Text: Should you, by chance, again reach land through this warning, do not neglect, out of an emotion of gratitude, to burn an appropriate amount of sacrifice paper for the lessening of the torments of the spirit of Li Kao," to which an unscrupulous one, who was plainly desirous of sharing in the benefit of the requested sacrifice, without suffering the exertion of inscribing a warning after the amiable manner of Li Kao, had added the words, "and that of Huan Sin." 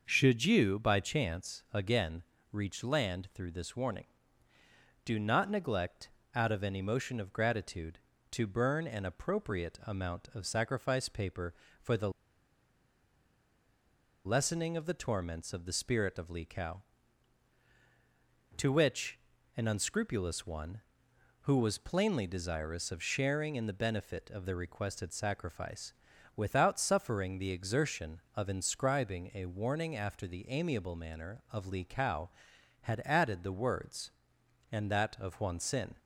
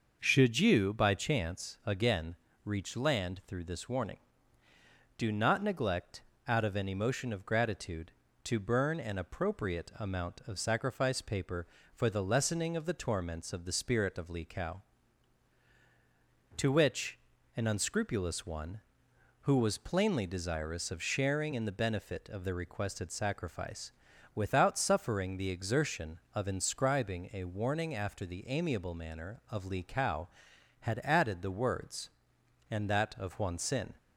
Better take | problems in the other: second | starts louder than the rest; noticeable; until 1.0 s; 6 dB; noticeable in the second // pauses between "again" and "reach"; slight; at 2.2 s; 0.30 s long; slight in the second // pauses between "the" and "lessening"; strong; at 12.0 s; 2.1 s long // pauses between "which" and "an"; at 19.1 s; 0.38 s long; also in the second

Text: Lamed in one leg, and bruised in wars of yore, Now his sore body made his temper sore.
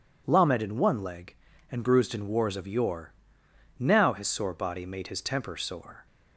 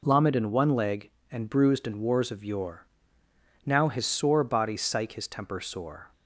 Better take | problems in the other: first | says "psych" for "made"; at 4.7 s

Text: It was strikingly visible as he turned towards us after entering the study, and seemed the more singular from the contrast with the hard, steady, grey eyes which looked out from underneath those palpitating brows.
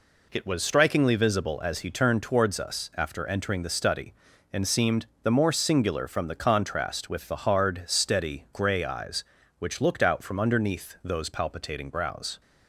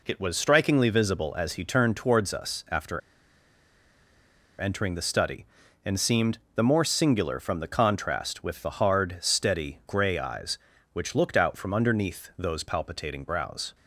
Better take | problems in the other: first | pauses between "after" and "entering"; strong; at 3.0 s; 1.5 s long // pauses between "seemed" and "the"; slight; at 6.3 s; 0.16 s long; slight in the first

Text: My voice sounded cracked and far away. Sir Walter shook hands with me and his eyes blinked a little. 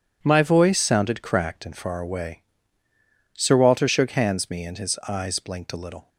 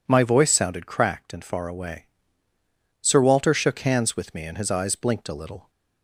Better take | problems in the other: second | skips "with"; at 4.5 s

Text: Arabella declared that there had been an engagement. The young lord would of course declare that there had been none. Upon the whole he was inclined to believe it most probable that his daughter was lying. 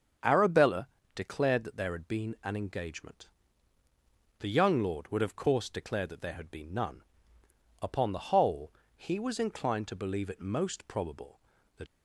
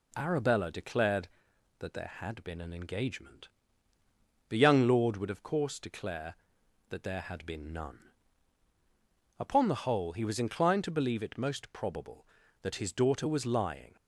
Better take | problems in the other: second | starts louder than the rest; strong; until 1.5 s; 7 dB // pauses between "Arabella" and "declared"; slight; at 0.8 s; 0.26 s long // pauses between "whole" and "he"; slight; at 8.7 s; 0.24 s long // stops before "his daughter was lying"; at 11.8 s

